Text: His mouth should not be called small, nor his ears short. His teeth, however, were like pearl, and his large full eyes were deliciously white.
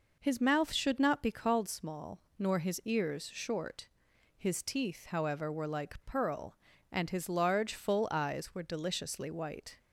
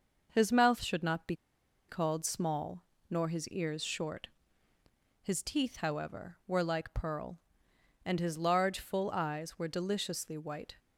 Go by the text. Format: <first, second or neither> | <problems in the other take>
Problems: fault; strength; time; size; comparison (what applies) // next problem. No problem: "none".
first | starts louder than the rest; noticeable; until 1.3 s; 6 dB // pauses between "be" and "called"; noticeable; at 1.3 s; 0.53 s long